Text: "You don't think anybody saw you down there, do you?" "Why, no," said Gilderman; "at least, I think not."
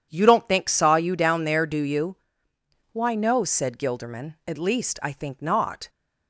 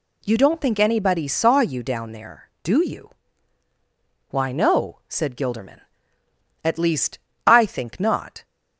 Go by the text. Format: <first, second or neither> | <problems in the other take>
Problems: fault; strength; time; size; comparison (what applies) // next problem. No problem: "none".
second | skips "anybody"; at 0.6 s